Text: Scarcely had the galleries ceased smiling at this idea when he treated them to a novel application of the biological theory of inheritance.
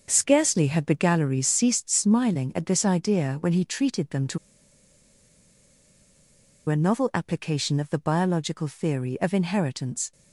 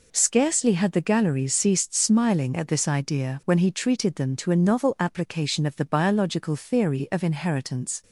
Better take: second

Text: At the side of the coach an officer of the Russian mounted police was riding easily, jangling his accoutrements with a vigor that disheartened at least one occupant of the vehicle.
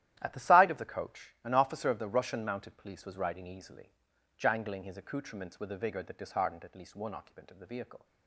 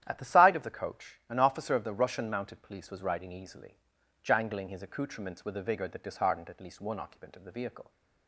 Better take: second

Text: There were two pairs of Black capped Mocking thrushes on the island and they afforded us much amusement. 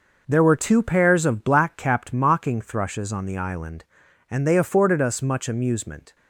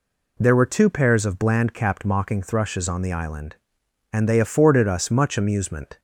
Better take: first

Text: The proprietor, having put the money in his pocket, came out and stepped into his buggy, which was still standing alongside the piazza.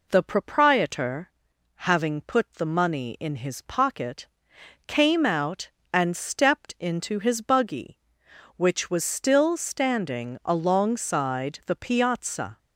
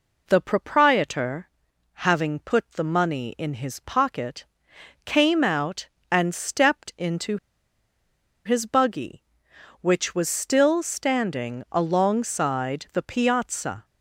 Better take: first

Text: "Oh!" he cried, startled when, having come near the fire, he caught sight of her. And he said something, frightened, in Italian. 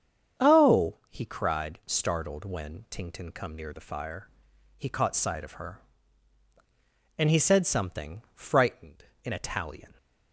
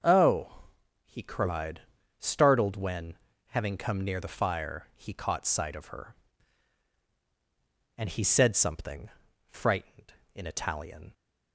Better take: second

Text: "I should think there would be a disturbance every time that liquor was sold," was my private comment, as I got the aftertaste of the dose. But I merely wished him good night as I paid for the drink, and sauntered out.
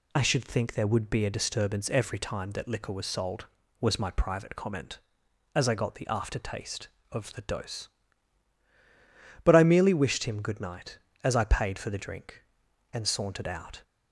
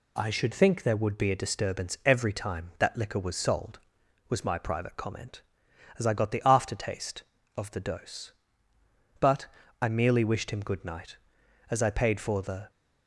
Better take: first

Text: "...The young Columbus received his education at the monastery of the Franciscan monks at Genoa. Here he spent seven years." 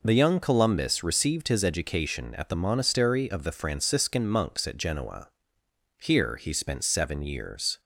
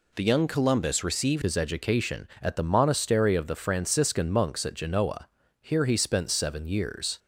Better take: first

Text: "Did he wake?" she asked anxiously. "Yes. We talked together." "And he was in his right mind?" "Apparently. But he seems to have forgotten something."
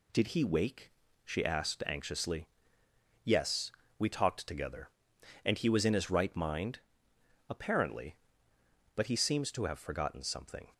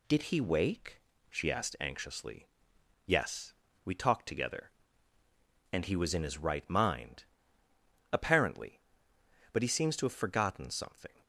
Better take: neither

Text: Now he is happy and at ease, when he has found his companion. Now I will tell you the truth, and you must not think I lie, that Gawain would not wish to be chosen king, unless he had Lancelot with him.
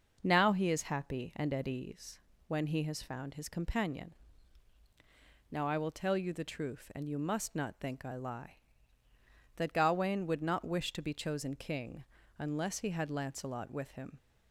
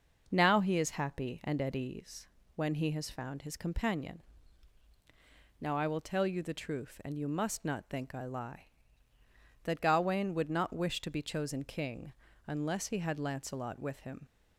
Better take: neither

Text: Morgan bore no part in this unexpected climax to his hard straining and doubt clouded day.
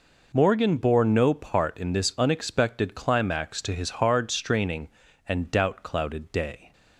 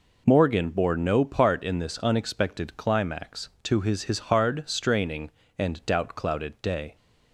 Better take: first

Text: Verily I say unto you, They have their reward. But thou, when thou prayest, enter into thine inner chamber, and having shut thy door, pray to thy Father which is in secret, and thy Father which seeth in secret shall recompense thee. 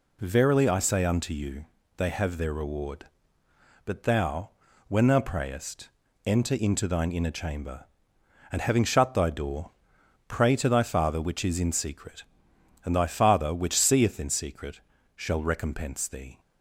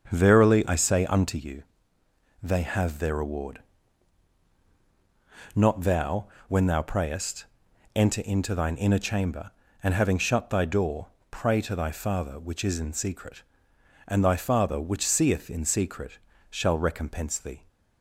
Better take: first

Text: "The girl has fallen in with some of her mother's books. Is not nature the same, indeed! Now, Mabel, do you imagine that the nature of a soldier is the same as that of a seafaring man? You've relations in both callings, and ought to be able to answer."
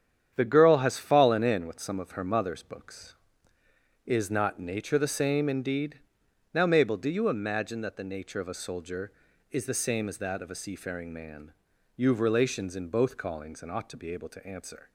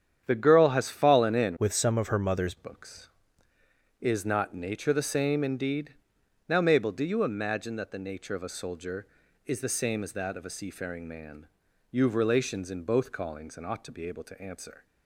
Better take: first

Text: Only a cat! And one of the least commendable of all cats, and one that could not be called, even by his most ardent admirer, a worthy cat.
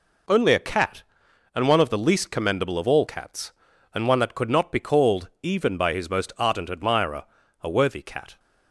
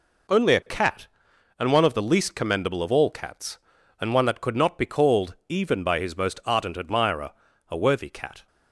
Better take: neither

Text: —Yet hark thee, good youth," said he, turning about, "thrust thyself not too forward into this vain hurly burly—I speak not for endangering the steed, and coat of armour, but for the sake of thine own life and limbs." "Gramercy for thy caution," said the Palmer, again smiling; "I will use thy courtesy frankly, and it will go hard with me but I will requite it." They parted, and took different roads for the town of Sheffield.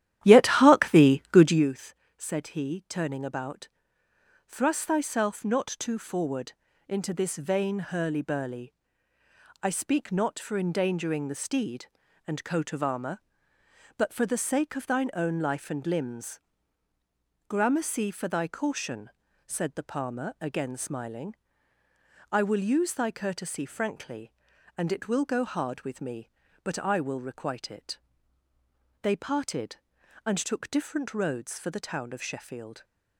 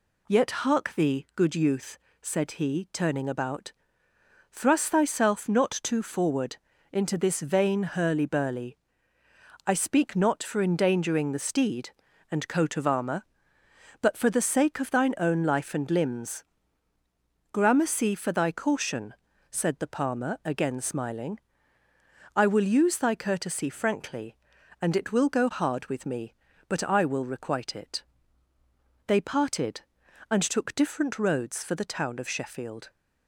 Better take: second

